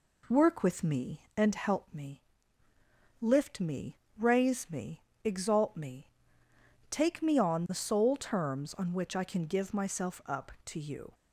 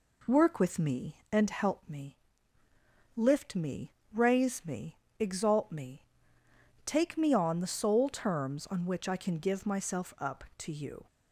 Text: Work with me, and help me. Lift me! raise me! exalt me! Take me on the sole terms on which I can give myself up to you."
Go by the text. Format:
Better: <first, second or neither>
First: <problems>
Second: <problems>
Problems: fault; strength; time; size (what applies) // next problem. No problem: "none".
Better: neither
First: none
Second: none